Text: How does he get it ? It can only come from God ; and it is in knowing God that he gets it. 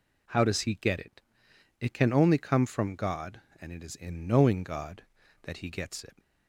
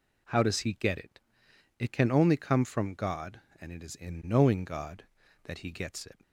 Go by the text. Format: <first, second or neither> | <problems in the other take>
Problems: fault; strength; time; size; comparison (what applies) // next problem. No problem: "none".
neither | none